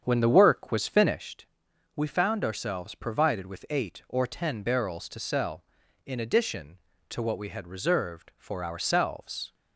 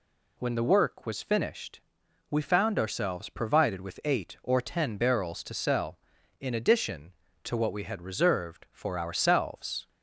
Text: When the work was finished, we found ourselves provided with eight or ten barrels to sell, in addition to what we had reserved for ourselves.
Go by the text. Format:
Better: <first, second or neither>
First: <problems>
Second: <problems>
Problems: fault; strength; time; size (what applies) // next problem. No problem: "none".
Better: second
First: starts louder than the rest; strong; until 1.3 s; 7.5 dB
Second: none